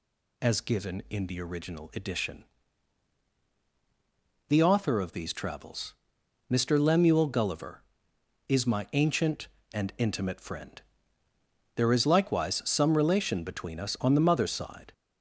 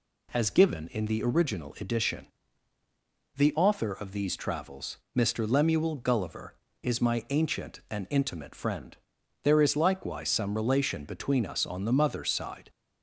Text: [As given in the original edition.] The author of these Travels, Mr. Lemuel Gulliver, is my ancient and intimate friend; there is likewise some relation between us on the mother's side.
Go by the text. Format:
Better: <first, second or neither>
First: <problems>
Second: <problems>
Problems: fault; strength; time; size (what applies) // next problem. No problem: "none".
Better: second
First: gets louder; noticeable; throughout; 4 dB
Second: none